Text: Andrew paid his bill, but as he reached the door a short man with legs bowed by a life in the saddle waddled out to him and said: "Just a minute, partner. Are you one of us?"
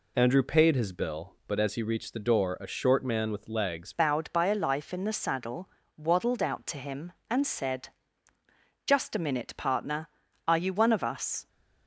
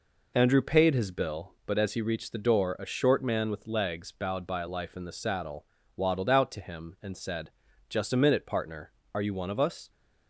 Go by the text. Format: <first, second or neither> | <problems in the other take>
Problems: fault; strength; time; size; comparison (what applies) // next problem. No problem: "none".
second | changes voice at "bowed"; from 3.9 s on; 7.5 s long // pauses between "saddle" and "waddled"; slight; at 5.6 s; 0.30 s long; slight in the second